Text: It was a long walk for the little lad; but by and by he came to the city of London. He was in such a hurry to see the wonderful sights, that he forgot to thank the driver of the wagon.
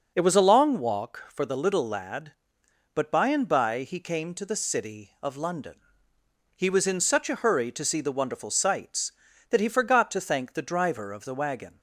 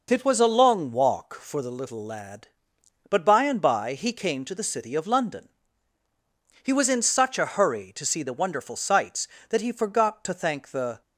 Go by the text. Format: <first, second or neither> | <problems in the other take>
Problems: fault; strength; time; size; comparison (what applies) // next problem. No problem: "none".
first | stops before "driver of the wagon"; at 11.0 s